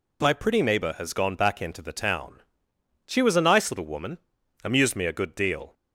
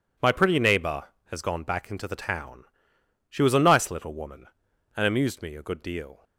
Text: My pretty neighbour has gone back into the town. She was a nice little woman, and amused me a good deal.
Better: second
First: skips "and"; at 4.4 s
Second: none

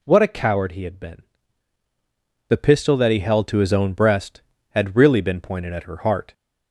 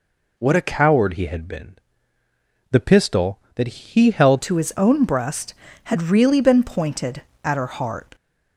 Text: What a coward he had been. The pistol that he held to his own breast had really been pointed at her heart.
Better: first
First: none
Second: changes voice at "to"; from 4.4 s on; 3.7 s long

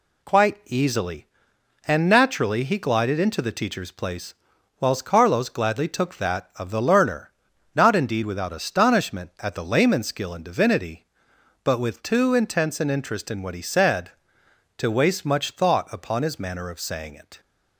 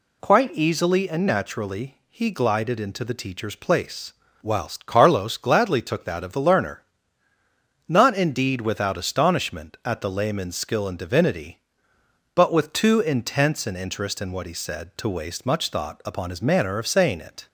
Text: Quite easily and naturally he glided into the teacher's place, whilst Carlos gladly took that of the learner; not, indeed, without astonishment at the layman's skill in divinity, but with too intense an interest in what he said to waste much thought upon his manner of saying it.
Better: neither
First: none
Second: none

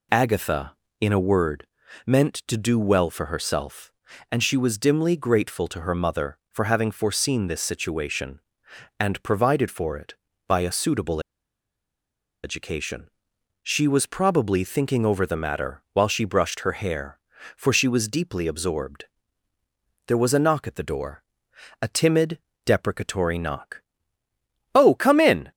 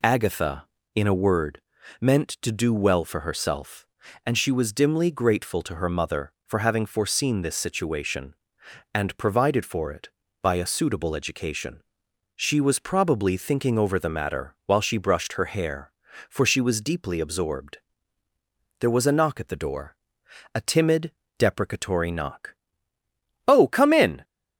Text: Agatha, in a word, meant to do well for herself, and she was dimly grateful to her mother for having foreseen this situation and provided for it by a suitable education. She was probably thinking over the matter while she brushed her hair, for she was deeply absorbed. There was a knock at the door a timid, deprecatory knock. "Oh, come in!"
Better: second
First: pauses between "suitable" and "education"; at 11.2 s; 1.2 s long // pauses between "door" and "a"; noticeable; at 21.2 s; 0.60 s long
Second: pauses between "door" and "a"; noticeable; at 19.9 s; 0.60 s long

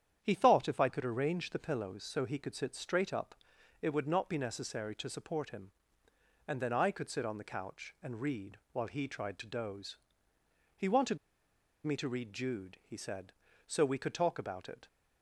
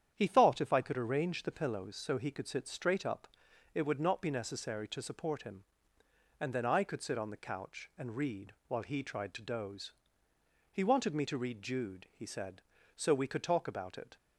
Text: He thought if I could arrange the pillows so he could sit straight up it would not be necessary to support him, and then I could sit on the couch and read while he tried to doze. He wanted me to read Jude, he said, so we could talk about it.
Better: second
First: starts louder than the rest; strong; until 1.2 s; 9 dB // pauses between "up" and "it"; noticeable; at 3.3 s; 0.46 s long // pauses between "wanted" and "me"; noticeable; at 11.1 s; 0.67 s long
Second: starts louder than the rest; strong; until 1.1 s; 9 dB // pauses between "up" and "it"; noticeable; at 3.2 s; 0.46 s long

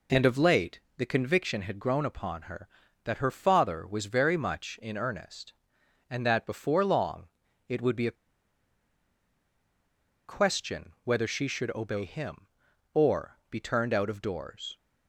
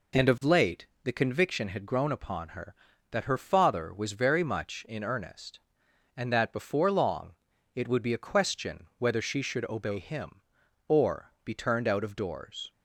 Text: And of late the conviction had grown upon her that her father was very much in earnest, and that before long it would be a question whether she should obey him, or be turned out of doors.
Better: second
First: pauses between "late" and "the"; slight; at 0.8 s; 0.16 s long // pauses between "long" and "it"; at 7.2 s; 0.40 s long // pauses between "a" and "question"; strong; at 8.1 s; 2.1 s long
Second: pauses between "late" and "the"; slight; at 0.8 s; 0.16 s long // pauses between "long" and "it"; at 7.3 s; 0.40 s long

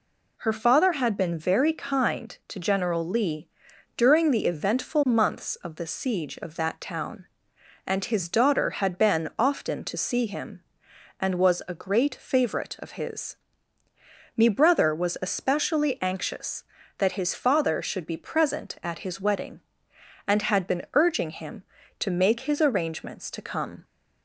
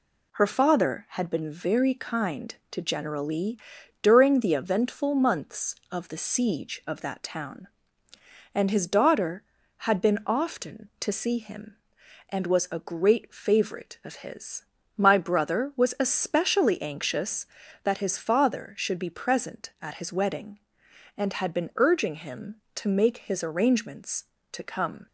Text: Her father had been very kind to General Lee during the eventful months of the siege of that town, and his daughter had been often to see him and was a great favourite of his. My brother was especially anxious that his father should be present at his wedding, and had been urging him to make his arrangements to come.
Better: second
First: pauses between "Lee" and "during"; noticeable; at 3.4 s; 0.48 s long // says "Me" for "My"; at 14.3 s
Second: pauses between "Lee" and "during"; at 3.5 s; 0.44 s long

